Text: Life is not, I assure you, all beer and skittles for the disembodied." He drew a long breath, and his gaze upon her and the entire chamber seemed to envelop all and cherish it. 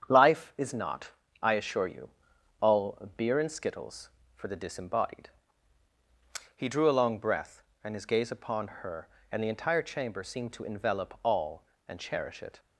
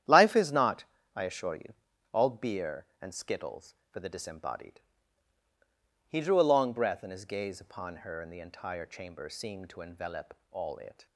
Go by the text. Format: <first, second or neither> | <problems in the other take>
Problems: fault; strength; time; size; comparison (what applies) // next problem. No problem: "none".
first | starts louder than the rest; strong; until 1.4 s; 10.5 dB; strong in the first // skips "and cherish"; at 10.7 s